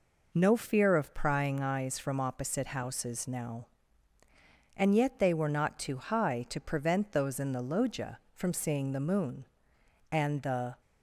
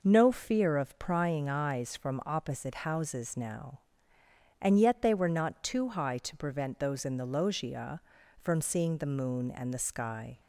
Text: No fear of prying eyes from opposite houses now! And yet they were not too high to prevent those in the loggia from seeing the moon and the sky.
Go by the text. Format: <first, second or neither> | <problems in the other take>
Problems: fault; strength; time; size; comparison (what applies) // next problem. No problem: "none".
second | stops before "sky"; at 10.8 s